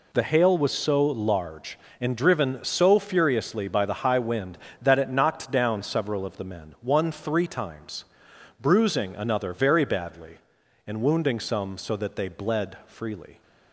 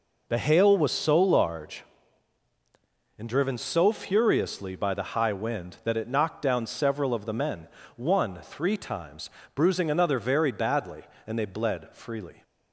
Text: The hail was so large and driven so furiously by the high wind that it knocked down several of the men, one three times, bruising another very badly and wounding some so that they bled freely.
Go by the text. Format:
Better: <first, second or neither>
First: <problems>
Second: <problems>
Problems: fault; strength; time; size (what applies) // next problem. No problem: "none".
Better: first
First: none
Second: skips "wounding some so that"; at 11.3 s